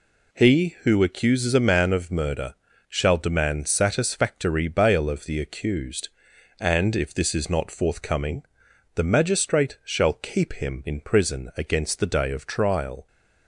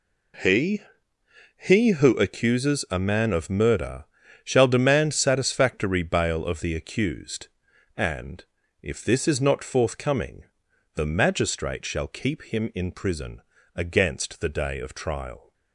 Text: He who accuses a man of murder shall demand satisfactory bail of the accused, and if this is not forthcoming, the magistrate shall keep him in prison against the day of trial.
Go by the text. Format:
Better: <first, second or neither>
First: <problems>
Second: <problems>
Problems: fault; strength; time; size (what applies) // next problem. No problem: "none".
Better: first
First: pauses between "murder" and "shall"; slight; at 2.5 s; 0.32 s long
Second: says "He" twice; at 1.5 s // pauses between "murder" and "shall"; at 4.0 s; 0.38 s long // pauses between "and" and "if"; at 8.4 s; 0.40 s long // pauses between "prison" and "against"; slight; at 13.4 s; 0.34 s long